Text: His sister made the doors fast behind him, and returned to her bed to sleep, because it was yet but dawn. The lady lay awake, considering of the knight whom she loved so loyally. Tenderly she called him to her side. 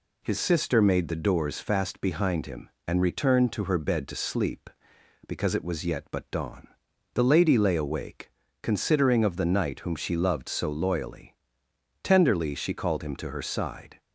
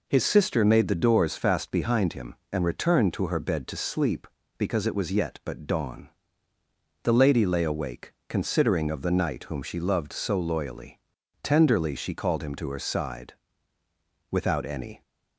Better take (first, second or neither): first